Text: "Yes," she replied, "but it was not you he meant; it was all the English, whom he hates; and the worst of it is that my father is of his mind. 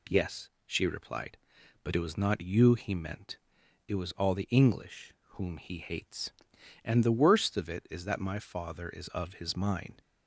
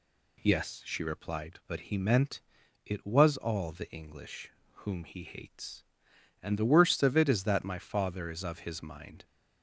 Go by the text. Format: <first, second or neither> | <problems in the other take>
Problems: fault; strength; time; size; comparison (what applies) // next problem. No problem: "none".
first | skips "it was not you"; at 1.8 s